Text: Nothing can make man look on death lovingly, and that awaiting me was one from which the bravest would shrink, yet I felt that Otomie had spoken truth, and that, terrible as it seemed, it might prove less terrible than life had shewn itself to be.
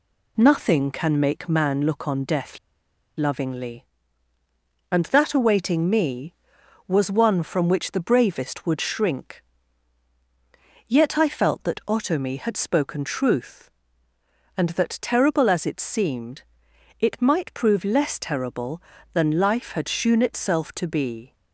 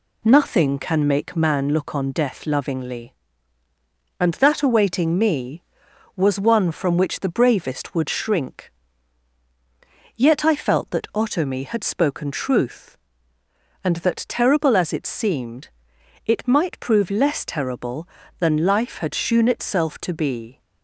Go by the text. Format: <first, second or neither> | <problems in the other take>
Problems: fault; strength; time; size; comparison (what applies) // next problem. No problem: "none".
second | pauses between "death" and "lovingly"; noticeable; at 2.5 s; 0.59 s long